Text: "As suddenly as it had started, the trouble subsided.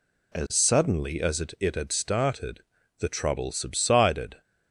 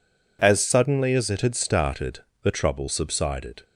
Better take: second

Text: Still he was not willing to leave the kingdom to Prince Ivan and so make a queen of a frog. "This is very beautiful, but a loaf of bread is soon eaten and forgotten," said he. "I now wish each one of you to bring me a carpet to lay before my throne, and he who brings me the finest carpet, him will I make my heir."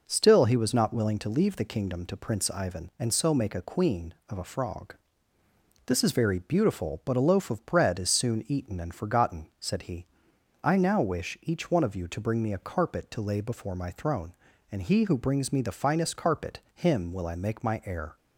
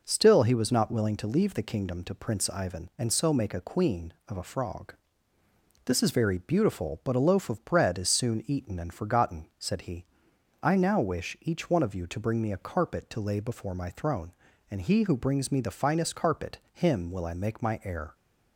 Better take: neither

